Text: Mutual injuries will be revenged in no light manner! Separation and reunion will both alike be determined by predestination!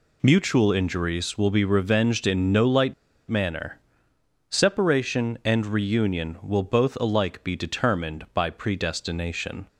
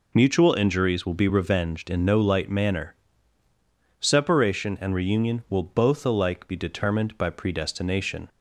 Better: second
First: pauses between "light" and "manner"; slight; at 2.9 s; 0.35 s long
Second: none

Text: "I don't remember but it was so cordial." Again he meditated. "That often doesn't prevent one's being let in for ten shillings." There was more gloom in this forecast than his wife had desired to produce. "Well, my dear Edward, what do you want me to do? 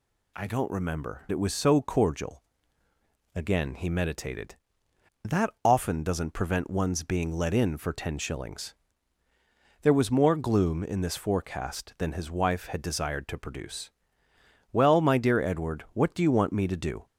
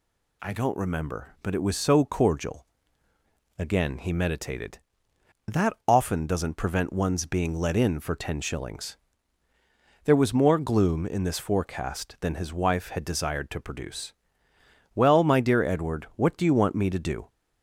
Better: second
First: skips "but"; at 1.2 s // pauses between "That" and "often"; slight; at 5.4 s; 0.16 s long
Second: pauses between "That" and "often"; slight; at 5.7 s; 0.16 s long

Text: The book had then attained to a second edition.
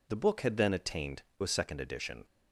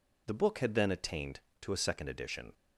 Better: second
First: skips "to"; at 1.3 s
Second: none

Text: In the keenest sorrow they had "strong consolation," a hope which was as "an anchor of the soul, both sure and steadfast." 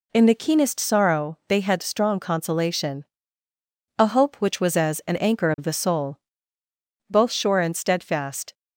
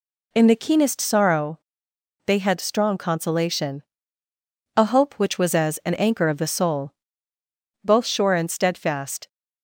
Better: first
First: none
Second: pauses between "sorrow" and "they"; noticeable; at 1.5 s; 0.66 s long

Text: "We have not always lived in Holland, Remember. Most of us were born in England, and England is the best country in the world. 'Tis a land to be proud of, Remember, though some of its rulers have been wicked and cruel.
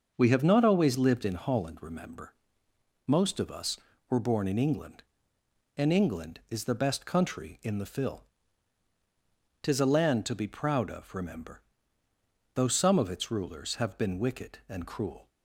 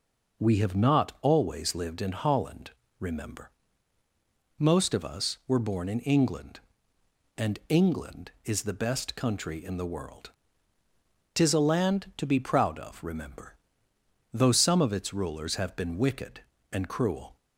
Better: second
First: starts louder than the rest; until 1.1 s; 6.5 dB // says "fill" for "world"; at 7.8 s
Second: none

